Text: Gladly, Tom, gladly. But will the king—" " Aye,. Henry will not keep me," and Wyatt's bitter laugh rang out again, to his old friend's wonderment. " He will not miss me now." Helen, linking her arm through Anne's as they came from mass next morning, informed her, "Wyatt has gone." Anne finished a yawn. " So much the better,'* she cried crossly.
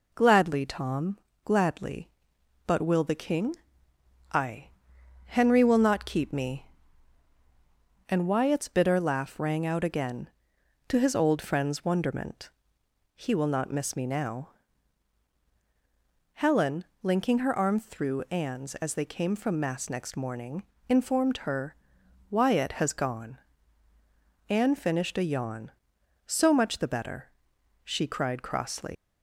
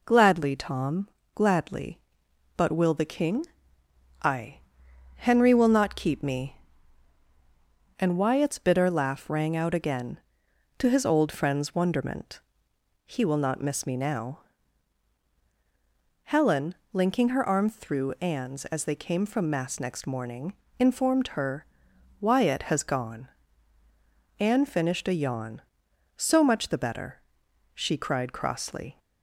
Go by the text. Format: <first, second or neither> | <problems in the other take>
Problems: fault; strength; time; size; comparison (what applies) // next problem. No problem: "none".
second | leaves "crossly" unfinished; at 28.9 s; 130 ms